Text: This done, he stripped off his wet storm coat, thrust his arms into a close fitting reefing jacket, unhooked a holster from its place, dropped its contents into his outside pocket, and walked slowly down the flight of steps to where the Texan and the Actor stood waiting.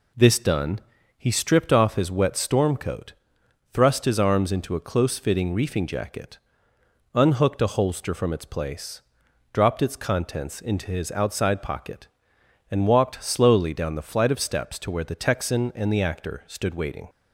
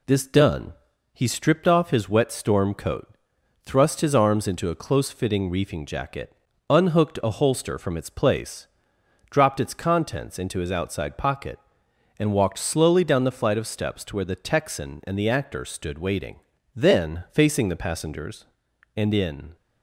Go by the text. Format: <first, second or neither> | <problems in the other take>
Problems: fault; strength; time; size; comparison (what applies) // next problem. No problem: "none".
first | goes on to say "Then facing the passengers and in"; strong; from 16.7 s on; 2.8 s long